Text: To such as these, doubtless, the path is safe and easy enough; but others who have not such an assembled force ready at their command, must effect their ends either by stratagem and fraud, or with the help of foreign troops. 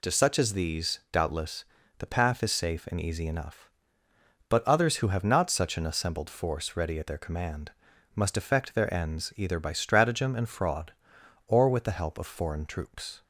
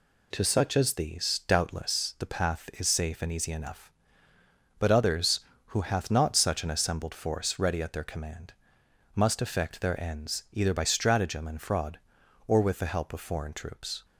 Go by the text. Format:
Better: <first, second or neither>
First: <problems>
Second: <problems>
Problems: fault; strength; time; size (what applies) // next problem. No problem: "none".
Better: first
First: none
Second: says "hath" for "have"; at 5.8 s